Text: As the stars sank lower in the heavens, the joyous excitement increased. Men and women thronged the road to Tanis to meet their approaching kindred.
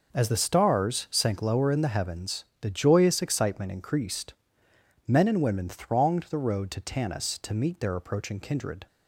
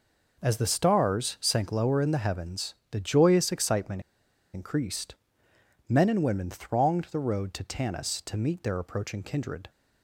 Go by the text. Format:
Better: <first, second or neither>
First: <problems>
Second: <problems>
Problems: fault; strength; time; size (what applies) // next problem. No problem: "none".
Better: first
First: none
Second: pauses between "excitement" and "increased"; noticeable; at 3.9 s; 0.53 s long